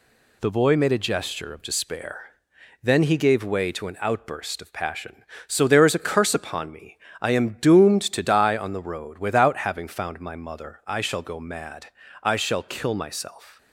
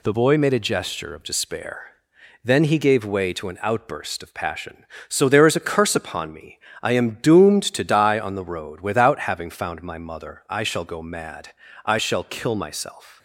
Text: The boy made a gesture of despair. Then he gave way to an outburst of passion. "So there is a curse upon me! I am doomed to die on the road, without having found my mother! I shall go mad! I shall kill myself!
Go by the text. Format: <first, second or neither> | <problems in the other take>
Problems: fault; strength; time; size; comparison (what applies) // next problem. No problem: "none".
neither | none